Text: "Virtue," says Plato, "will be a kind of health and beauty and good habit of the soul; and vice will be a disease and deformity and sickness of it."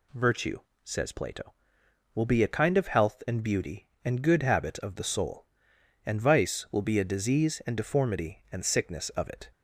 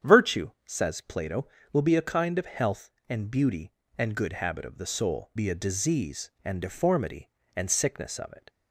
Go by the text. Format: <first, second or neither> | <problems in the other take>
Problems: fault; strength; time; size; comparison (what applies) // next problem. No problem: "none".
first | starts louder than the rest; strong; until 1.1 s; 8.5 dB // skips "and vice will"; at 5.3 s